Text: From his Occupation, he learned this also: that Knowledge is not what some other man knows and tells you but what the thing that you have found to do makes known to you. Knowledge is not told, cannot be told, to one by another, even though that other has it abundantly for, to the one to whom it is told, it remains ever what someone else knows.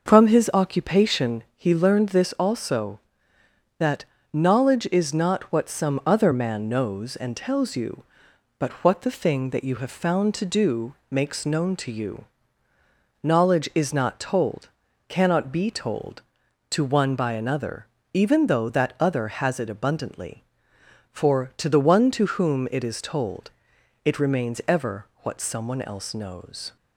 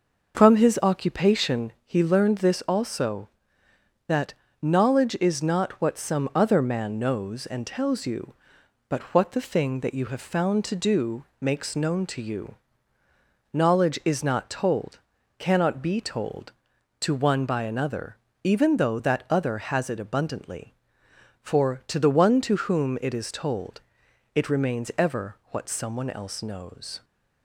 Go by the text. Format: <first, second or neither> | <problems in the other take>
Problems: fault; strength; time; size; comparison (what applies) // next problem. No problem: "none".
neither | pauses between "that" and "Knowledge"; slight; the same in both // pauses between "do" and "makes"; slight; the same in both // pauses between "ever" and "what"; slight; the same in both